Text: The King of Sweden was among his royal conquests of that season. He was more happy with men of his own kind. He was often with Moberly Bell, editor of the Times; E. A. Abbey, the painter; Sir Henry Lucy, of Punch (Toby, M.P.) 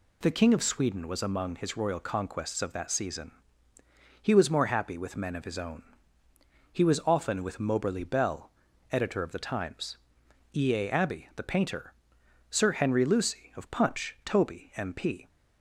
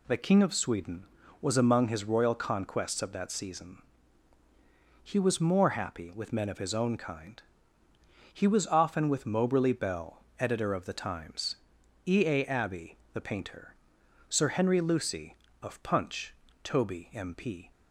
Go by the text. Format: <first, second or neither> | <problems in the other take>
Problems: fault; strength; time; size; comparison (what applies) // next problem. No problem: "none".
second | skips "kind"; at 6.2 s